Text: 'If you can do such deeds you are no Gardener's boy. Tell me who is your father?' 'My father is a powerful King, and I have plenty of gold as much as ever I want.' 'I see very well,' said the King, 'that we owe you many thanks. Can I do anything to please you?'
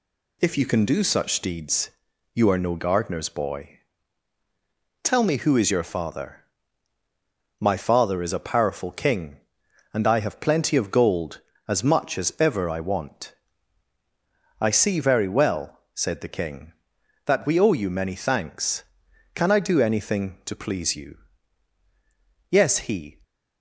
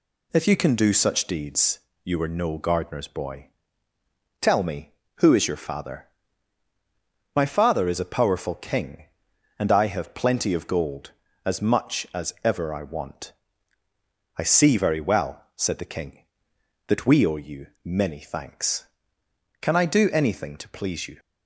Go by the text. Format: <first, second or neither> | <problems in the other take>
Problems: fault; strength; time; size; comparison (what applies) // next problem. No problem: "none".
second | pauses between "deeds" and "you"; at 1.8 s; 0.42 s long; slight in the second // goes on to say "Yes he"; noticeable; from 22.5 s on; 0.70 s long